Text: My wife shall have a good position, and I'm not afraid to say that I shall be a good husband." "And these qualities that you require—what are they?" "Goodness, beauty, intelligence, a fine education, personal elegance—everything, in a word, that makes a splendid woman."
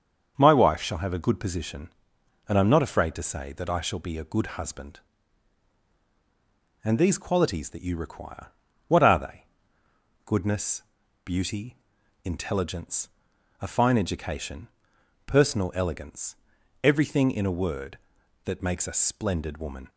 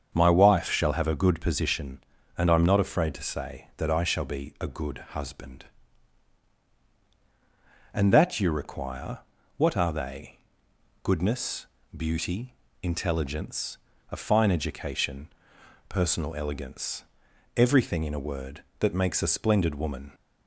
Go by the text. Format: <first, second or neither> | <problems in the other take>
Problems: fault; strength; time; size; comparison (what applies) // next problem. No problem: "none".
first | starts louder than the rest; strong; until 1.1 s; 7.5 dB; also in the first // pauses between "good" and "husband"; slight; at 4.9 s; 0.16 s long // skips "these qualities"; at 8.1 s